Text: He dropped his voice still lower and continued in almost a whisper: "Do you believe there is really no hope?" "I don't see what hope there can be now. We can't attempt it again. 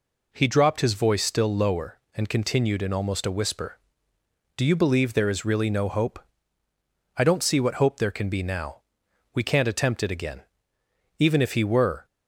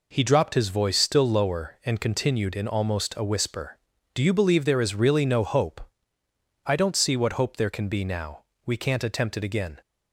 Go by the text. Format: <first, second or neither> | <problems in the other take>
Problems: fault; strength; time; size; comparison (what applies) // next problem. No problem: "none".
second | goes on to say "Even if he were"; noticeable; from 11.1 s on; 0.88 s long